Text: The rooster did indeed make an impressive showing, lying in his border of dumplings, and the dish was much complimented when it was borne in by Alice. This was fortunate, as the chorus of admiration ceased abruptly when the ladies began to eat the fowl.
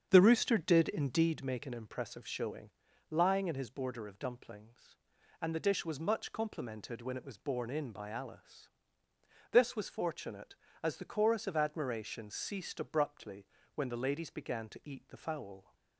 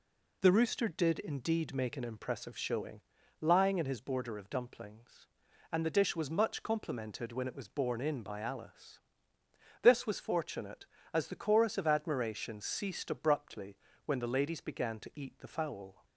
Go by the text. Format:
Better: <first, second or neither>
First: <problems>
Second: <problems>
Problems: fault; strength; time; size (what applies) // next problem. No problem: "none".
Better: second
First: starts louder than the rest; strong; until 1.4 s; 7.5 dB // pauses between "abruptly" and "when"; slight; at 13.4 s; 0.28 s long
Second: pauses between "abruptly" and "when"; slight; at 13.7 s; 0.28 s long